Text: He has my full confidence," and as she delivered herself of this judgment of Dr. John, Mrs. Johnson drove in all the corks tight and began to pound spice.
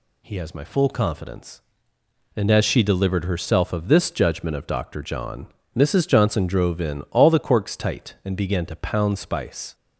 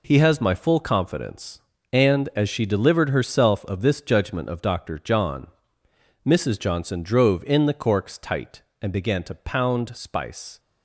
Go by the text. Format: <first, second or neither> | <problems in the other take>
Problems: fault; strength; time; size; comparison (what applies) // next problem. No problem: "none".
first | skips "all"; at 7.6 s